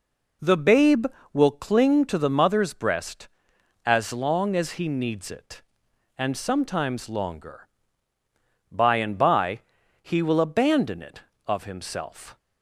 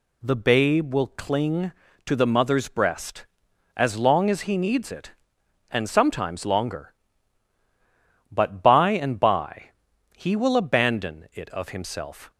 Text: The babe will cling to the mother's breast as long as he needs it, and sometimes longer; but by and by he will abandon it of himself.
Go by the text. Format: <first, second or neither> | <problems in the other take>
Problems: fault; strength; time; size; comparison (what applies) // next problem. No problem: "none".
second | skips "but"; at 8.1 s // pauses between "by" and "he"; at 9.5 s; 0.42 s long; also in the second